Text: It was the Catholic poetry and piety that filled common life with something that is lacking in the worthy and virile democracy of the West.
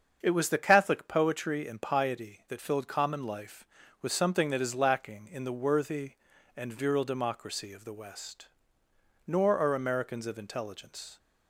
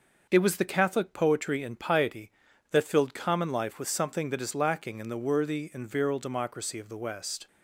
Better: second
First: starts louder than the rest; until 1.2 s; 7 dB // goes on to say "Nor are Americans of intelligence"; strong; from 9.2 s on; 1.9 s long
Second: none

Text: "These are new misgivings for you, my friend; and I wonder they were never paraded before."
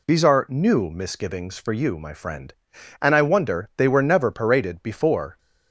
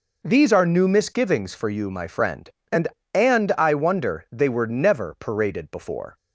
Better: first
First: none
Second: says "and" twice; at 3.1 s

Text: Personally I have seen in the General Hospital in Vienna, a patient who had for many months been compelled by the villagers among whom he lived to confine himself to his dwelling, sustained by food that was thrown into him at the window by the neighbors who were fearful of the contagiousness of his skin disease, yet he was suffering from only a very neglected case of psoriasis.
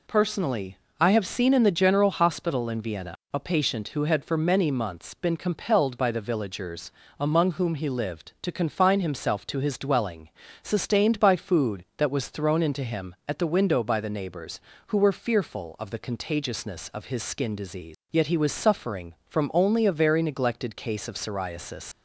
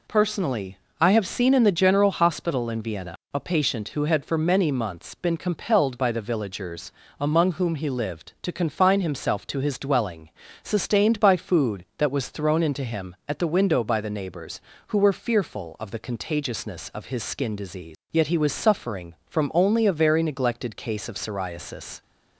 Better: second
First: pauses between "Personally" and "I"; slight; at 0.7 s; 0.22 s long // pauses between "villagers" and "among"; slight; at 6.9 s; 0.30 s long // leaves "psoriasis" unfinished; at 21.9 s; 90 ms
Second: pauses between "Personally" and "I"; slight; at 0.7 s; 0.22 s long // pauses between "villagers" and "among"; slight; at 6.9 s; 0.30 s long

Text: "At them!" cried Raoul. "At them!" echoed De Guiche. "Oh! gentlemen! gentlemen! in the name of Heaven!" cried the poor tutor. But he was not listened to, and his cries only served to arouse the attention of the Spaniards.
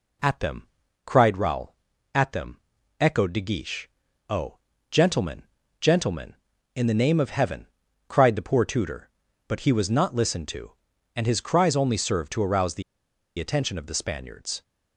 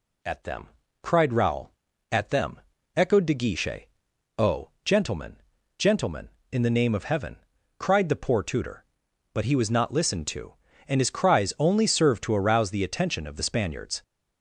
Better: second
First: pauses between "the" and "attention"; noticeable; at 12.8 s; 0.55 s long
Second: none

